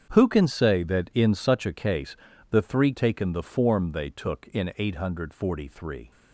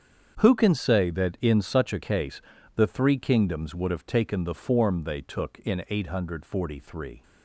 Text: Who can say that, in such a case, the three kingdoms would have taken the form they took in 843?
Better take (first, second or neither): second